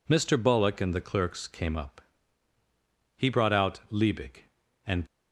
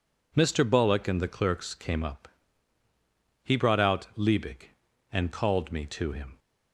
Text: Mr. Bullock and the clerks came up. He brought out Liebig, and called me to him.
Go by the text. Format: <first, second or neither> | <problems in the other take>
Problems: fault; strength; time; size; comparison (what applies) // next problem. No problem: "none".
second | stops before "called me to him"; at 5.0 s